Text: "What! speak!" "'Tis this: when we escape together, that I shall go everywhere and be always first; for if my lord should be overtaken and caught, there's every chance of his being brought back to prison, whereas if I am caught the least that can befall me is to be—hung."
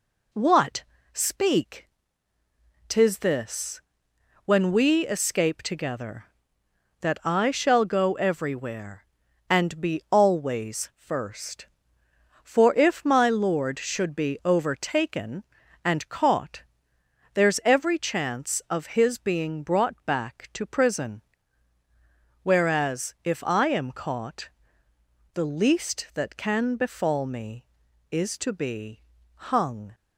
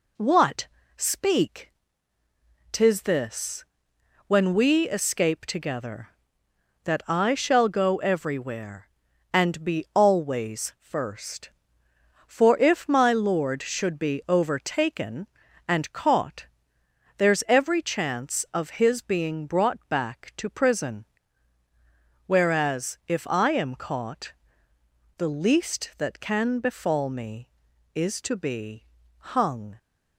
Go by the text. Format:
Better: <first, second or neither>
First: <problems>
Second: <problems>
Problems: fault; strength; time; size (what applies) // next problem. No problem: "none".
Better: neither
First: pauses between "caught" and "the"; noticeable; at 24.4 s; 0.86 s long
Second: pauses between "caught" and "the"; noticeable; at 24.3 s; 0.86 s long